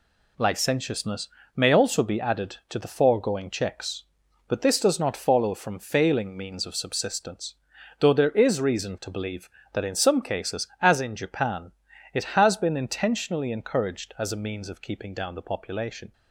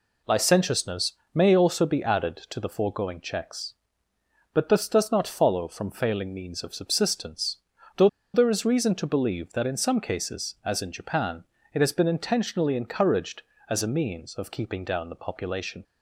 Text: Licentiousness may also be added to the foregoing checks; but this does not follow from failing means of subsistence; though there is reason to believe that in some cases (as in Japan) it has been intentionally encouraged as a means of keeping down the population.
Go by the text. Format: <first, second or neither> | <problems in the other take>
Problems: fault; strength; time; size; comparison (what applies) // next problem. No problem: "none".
first | pauses between "Licentiousness" and "may"; slight; at 1.1 s; 0.22 s long; slight in the first // pauses between "though" and "there"; slight; at 8.0 s; 0.27 s long